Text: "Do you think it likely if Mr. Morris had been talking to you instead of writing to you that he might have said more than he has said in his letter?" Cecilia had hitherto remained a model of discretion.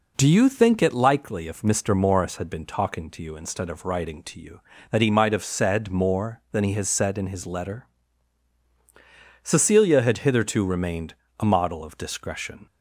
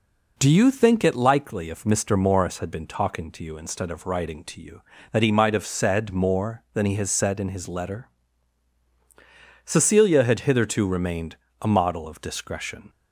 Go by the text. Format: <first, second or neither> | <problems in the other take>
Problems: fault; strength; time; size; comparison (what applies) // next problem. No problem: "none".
neither | pauses between "remained" and "a"; slight; the same in both